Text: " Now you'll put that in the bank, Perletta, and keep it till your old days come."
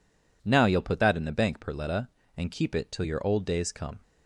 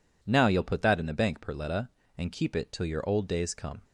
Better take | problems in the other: neither | none

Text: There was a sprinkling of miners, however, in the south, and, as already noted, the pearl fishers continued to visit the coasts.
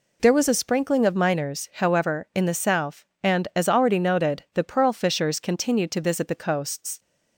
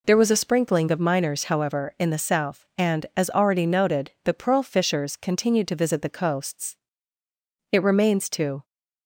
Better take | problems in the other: first | goes on to say "It remains to"; noticeable; from 7.7 s on; 0.92 s long

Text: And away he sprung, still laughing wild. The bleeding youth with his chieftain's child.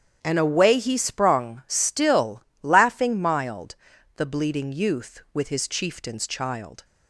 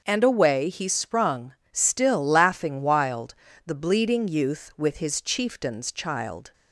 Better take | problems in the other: second | starts louder than the rest; strong; until 1.2 s; 9 dB; also in the second // pauses between "still" and "laughing"; slight; at 2.4 s; 0.20 s long // says "mild" for "wild"; at 3.2 s

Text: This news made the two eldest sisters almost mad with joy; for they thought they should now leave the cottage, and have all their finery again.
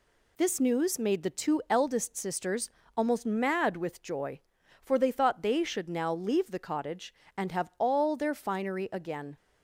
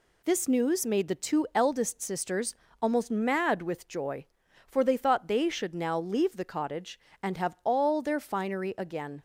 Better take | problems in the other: neither | pauses between "sisters" and "almost"; slight; the same in both

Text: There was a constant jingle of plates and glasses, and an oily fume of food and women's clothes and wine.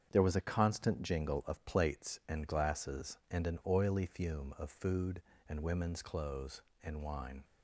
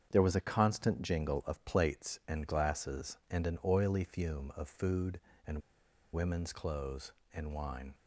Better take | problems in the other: first | starts louder than the rest; strong; until 1.1 s; 7.5 dB; strong in the first // pauses between "and" and "women's"; noticeable; at 5.5 s; 0.54 s long

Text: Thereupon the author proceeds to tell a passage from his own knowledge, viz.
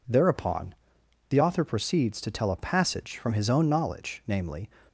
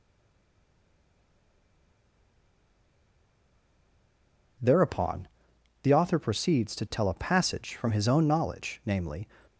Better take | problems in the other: first | stays silent before the first word; strong; until 4.5 s; 4.5 s long // pauses between "Thereupon" and "the"; noticeable; at 5.2 s; 0.56 s long; noticeable in the first

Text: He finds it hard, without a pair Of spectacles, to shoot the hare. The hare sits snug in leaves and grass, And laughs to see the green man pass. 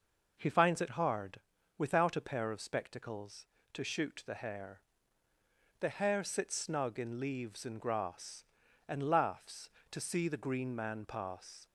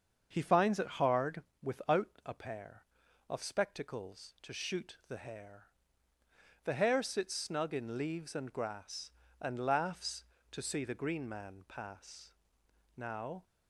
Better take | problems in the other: first | starts louder than the rest; until 1.3 s; 7 dB // goes on to say "Now"; slight; from 12.9 s on; 0.48 s long

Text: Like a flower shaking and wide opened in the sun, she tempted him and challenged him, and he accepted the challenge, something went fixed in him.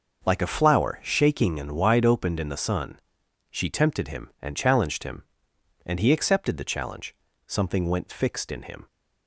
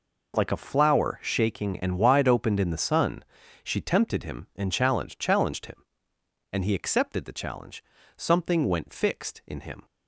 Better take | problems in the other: first | says "challenged" twice; at 5.1 s

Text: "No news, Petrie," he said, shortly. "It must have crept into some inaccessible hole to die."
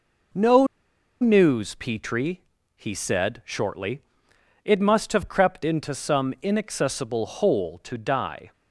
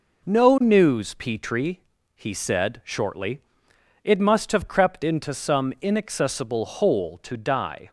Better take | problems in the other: second | pauses between "No" and "news"; noticeable; at 0.6 s; 0.55 s long

